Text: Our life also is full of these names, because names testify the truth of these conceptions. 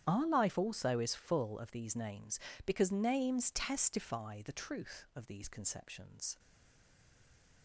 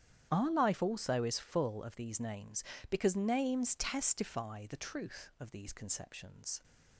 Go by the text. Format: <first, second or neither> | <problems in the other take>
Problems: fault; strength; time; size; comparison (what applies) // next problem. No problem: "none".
second | starts louder than the rest; strong; until 1.0 s; 10 dB; strong in the second // stays silent after the last word; noticeable; from 6.3 s on; 1.3 s long